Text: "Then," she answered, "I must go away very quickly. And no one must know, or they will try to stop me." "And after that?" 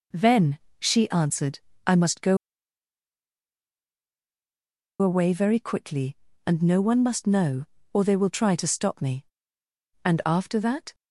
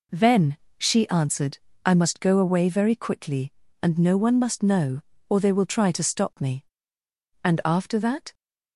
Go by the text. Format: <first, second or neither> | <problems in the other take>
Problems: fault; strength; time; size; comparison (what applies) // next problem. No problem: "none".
second | pauses between "go" and "away"; strong; at 2.3 s; 2.6 s long